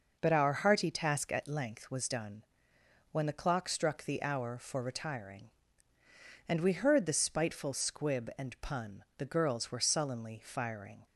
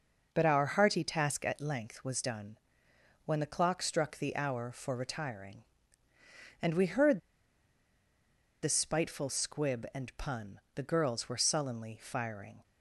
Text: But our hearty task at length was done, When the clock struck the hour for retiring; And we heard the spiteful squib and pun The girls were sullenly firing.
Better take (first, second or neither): first